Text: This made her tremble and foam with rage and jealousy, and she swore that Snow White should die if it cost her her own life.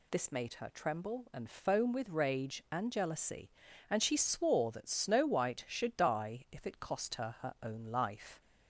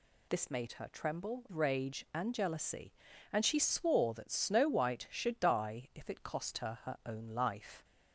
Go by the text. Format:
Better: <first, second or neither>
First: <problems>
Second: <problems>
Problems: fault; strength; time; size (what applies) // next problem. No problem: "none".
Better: first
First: none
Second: skips "and foam with"; at 1.4 s